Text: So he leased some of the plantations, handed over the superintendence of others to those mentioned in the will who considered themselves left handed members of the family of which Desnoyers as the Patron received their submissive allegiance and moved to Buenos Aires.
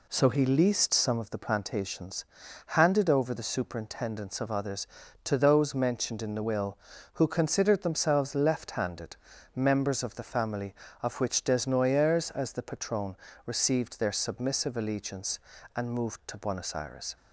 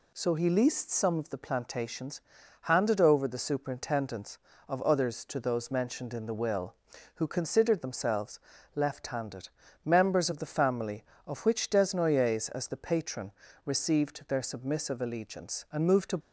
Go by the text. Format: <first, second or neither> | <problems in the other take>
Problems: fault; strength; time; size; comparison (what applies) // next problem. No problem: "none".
first | pauses between "themselves" and "left"; at 8.3 s; 0.38 s long // pauses between "handed" and "members"; slight; at 9.4 s; 0.36 s long; also in the first // pauses between "Patron" and "received"; slight; at 13.3 s; 0.32 s long; slight in the first // stops before "Buenos Aires"; at 16.2 s